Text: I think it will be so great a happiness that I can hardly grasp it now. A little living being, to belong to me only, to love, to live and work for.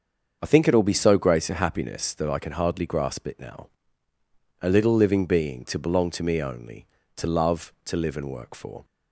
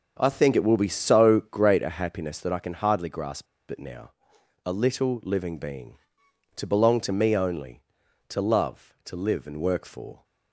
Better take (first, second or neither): first